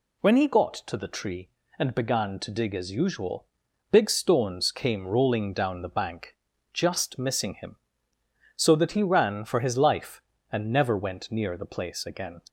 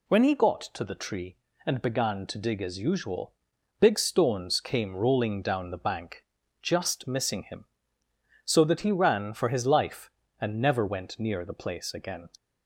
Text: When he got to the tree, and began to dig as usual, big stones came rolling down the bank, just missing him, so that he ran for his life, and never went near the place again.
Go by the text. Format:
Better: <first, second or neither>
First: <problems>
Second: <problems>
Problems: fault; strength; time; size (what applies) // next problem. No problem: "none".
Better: neither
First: none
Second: none